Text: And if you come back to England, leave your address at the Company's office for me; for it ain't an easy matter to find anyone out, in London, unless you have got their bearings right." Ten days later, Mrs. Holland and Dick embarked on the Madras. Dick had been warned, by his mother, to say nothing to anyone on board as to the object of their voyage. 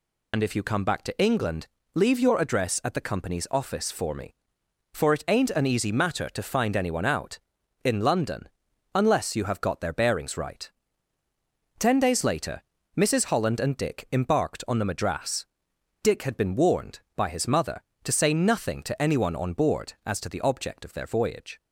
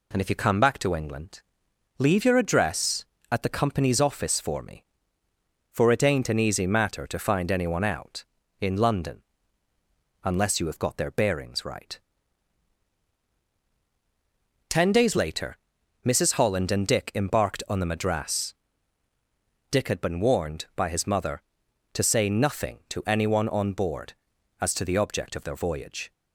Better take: second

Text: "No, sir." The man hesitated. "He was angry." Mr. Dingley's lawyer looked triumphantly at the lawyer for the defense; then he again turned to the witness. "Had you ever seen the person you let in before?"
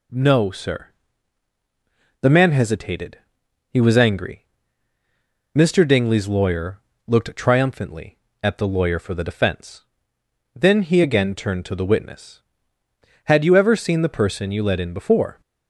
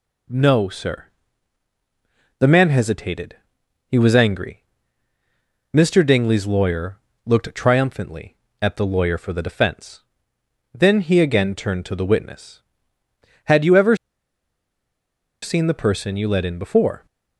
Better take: first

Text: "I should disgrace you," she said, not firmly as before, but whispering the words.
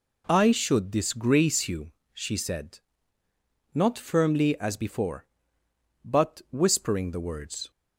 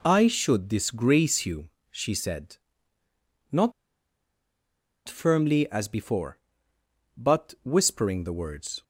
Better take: first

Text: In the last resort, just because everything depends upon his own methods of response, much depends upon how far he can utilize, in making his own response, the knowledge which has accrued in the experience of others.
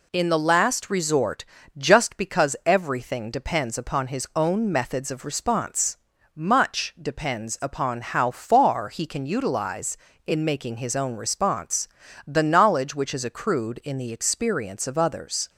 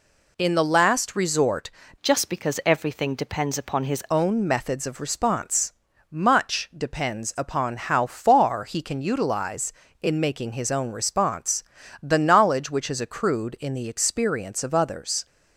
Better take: first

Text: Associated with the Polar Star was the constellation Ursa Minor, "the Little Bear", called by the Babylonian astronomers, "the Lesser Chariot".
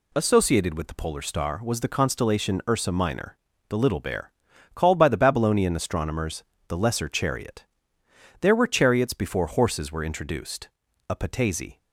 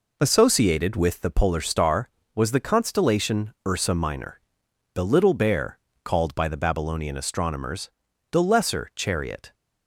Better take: second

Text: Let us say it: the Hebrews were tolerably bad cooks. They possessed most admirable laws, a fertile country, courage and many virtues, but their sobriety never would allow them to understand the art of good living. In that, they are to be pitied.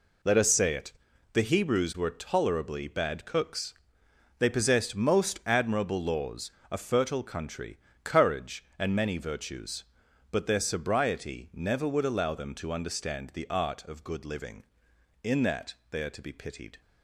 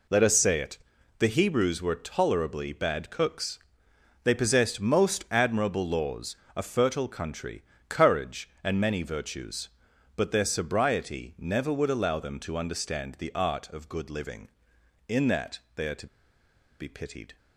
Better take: first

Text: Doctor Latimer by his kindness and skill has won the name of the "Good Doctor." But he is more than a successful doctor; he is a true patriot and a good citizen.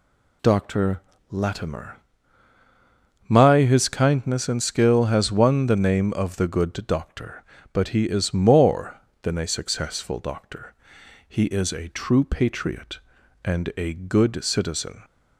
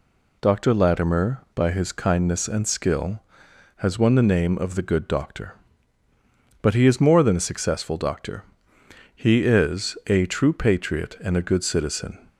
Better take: second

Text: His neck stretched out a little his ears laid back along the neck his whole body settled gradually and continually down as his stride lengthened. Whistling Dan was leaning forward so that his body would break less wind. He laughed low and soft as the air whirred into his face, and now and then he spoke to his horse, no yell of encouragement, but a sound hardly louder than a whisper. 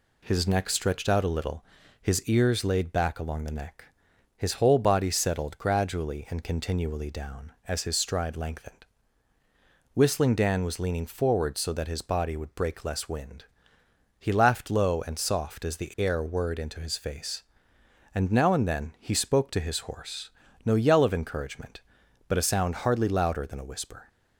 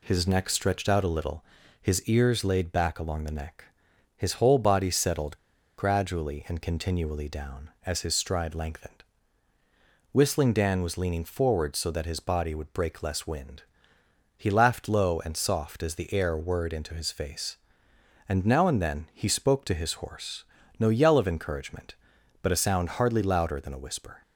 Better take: first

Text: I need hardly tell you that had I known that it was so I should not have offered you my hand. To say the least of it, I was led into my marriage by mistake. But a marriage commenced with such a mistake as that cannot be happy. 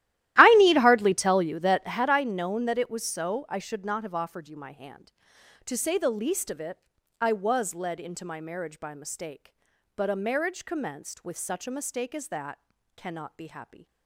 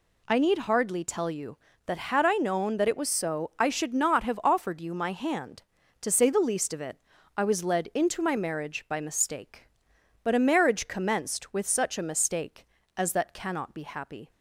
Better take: second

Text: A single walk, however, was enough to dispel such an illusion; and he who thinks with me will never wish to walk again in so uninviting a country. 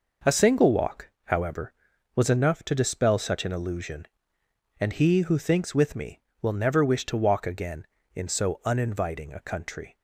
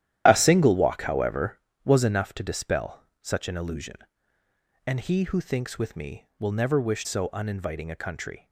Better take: first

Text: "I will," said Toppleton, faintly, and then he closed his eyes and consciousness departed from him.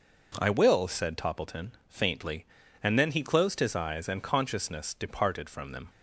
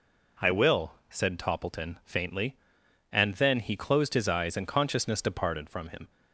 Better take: second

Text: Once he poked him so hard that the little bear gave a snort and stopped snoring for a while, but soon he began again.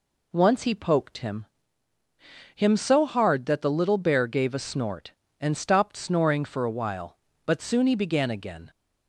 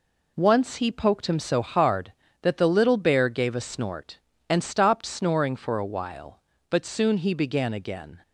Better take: second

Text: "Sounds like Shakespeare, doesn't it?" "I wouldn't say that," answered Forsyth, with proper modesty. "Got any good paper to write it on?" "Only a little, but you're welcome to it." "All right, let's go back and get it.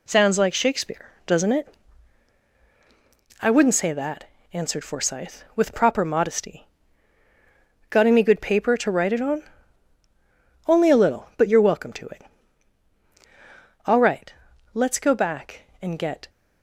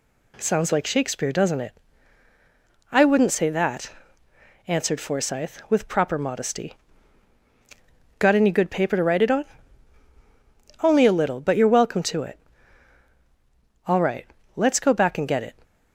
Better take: second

